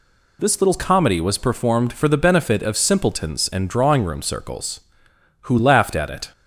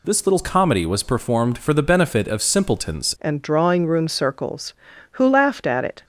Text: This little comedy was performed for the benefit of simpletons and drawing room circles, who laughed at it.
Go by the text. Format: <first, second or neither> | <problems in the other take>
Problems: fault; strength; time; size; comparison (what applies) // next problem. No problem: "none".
first | changes voice at "and"; from 3.1 s on; 2.9 s long